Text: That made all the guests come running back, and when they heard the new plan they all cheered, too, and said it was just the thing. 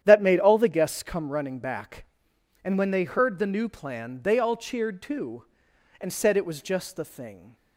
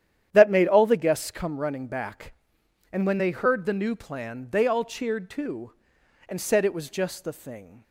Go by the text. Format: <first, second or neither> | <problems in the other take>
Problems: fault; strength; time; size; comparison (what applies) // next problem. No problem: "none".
neither | starts louder than the rest; strong; the same in both